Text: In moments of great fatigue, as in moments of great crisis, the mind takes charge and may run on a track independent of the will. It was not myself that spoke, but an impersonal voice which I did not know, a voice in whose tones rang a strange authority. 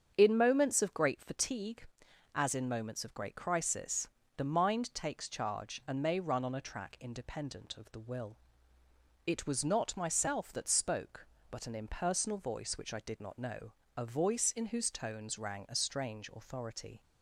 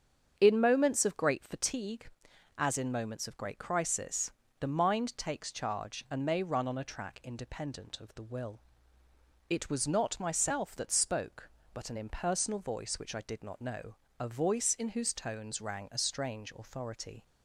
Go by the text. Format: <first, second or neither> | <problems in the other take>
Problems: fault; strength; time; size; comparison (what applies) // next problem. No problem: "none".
neither | starts louder than the rest; strong; the same in both